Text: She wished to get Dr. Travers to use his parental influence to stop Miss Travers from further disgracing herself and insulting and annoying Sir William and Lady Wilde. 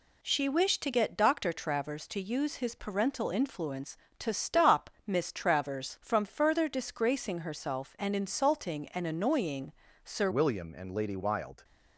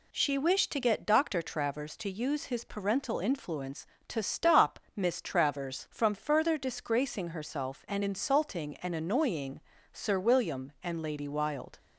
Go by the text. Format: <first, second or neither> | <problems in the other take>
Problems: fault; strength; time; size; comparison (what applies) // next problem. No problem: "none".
second | pauses between "stop" and "Miss"; slight; at 4.9 s; 0.16 s long; slight in the second // pauses between "annoying" and "Sir"; slight; at 9.7 s; 0.32 s long; slight in the second // changes voice at "William"; from 10.3 s on; 1.3 s long